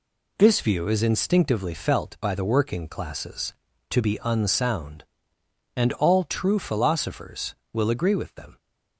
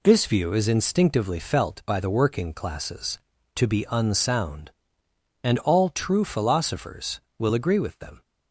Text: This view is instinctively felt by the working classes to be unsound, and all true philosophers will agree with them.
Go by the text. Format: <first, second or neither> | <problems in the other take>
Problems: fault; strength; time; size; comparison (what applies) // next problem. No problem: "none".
neither | none